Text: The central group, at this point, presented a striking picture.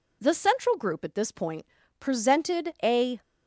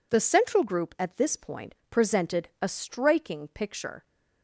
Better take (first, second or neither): second